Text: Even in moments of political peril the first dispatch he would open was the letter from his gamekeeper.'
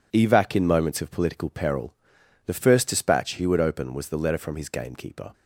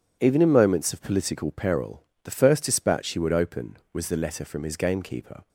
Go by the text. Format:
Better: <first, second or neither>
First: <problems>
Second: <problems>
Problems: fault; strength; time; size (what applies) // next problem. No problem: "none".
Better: second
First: says "Evac" for "Even"; at 0.1 s // pauses between "peril" and "the"; noticeable; at 1.9 s; 0.52 s long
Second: pauses between "peril" and "the"; slight; at 2.0 s; 0.22 s long